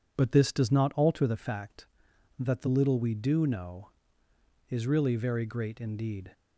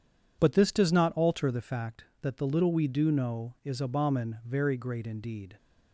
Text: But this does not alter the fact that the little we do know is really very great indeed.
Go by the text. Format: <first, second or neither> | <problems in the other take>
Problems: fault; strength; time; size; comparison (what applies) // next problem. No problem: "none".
first | says "abomin" for "really"; at 3.8 s